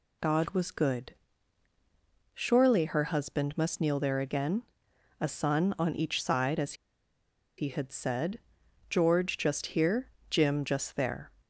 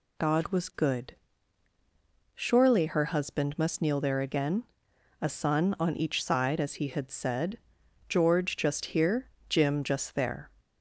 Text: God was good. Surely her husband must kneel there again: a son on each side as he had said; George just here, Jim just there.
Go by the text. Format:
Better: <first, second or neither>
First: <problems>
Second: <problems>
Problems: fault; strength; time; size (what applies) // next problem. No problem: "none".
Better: second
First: pauses between "as" and "he"; noticeable; at 6.7 s; 0.84 s long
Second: none